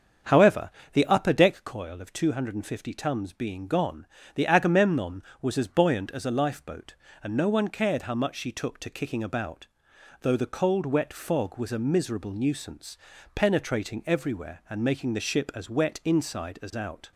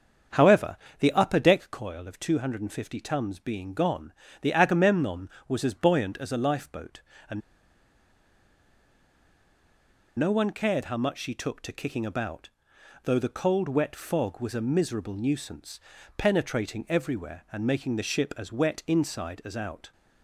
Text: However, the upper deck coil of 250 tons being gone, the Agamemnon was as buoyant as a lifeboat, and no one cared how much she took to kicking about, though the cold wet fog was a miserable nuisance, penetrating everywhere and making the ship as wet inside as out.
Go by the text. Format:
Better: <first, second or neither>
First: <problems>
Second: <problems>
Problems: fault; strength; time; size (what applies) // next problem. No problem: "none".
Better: first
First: starts louder than the rest; strong; until 1.4 s; 7.5 dB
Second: starts louder than the rest; strong; until 1.5 s; 7.5 dB // pauses between "and" and "no"; strong; at 7.4 s; 2.7 s long